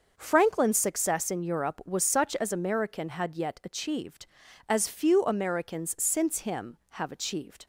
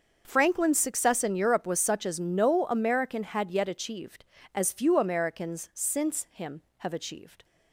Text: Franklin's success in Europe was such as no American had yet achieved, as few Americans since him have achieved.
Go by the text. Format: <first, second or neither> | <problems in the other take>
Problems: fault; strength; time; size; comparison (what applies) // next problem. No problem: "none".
second | starts louder than the rest; until 1.1 s; 6 dB; also in the second // skips "no"; at 2.5 s